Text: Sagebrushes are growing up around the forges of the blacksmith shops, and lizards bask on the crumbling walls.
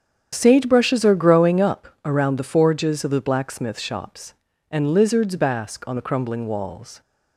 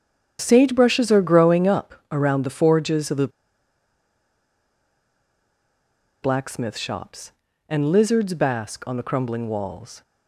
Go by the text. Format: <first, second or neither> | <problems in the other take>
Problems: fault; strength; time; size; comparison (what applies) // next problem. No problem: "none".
first | starts louder than the rest; strong; until 1.4 s; 8.5 dB; strong in the first // pauses between "the" and "blacksmith"; strong; at 3.2 s; 2.9 s long